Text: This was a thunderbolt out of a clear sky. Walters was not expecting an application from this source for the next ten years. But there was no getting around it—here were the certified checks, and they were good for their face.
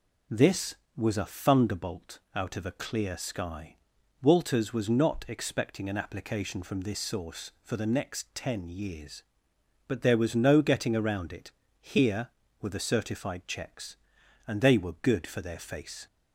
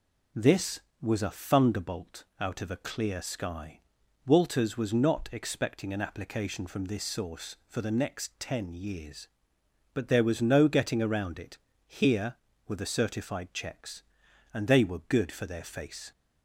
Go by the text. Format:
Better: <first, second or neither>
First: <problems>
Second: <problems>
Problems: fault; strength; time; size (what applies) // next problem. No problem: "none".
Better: neither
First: pauses between "thunderbolt" and "out"; slight; at 2.1 s; 0.16 s long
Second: pauses between "thunderbolt" and "out"; slight; at 2.2 s; 0.16 s long